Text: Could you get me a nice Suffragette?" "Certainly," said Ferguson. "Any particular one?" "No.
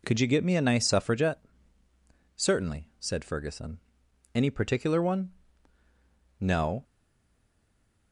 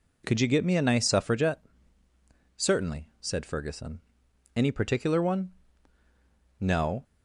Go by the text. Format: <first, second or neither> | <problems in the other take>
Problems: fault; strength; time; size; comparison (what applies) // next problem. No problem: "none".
second | stays silent after the last word; noticeable; from 6.8 s on; 1.3 s long